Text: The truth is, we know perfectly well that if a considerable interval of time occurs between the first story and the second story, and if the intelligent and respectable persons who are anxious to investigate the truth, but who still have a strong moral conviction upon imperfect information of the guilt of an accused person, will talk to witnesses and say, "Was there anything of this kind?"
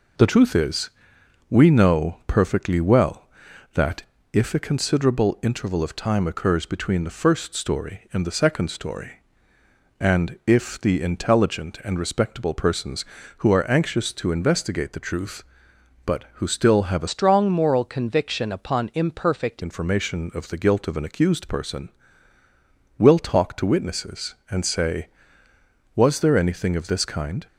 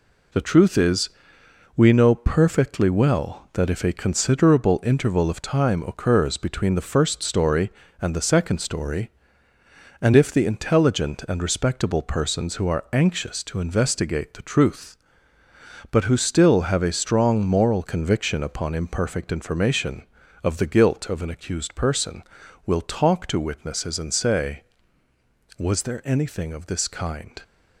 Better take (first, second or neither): second